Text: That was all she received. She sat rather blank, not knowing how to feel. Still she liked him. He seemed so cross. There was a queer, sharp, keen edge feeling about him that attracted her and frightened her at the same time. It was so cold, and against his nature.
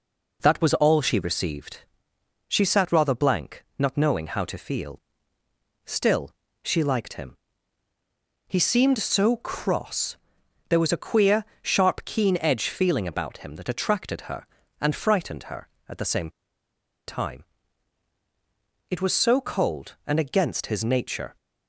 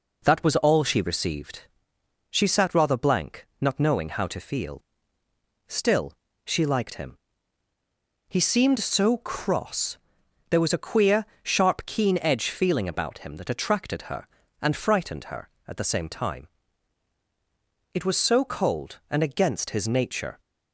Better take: second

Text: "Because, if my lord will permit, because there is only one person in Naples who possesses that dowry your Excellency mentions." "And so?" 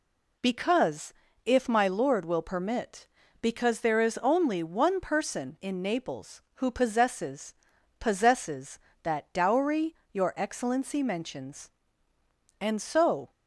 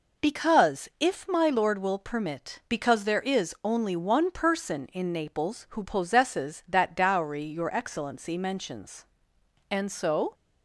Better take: second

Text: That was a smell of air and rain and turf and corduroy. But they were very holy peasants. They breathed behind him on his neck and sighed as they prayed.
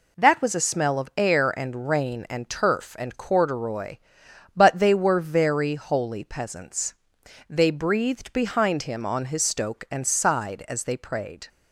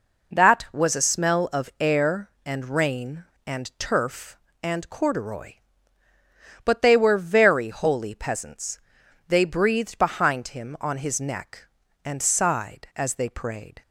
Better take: second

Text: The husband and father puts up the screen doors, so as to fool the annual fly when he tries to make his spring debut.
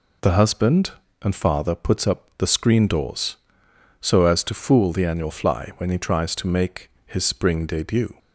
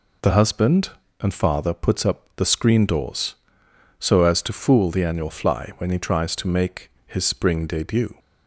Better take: neither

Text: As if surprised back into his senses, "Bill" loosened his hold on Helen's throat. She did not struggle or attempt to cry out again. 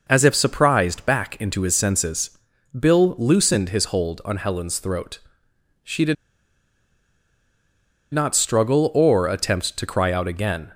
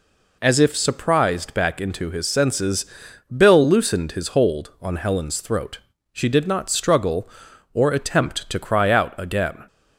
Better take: second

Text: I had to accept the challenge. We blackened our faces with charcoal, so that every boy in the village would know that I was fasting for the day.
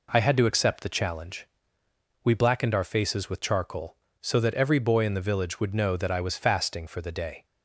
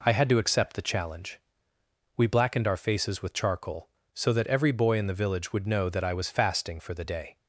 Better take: neither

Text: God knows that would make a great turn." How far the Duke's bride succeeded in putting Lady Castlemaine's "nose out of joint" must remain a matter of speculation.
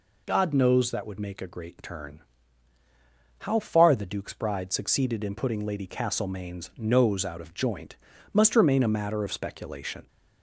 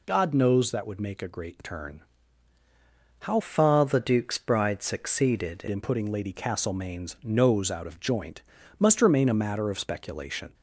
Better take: first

